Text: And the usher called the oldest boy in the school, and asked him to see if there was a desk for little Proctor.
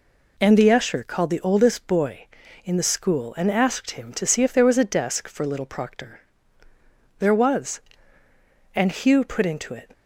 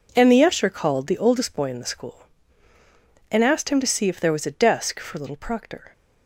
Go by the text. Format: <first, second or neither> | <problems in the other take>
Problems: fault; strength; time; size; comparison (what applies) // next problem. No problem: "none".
second | goes on to say "There was and Hugh put into it"; strong; from 7.1 s on; 2.7 s long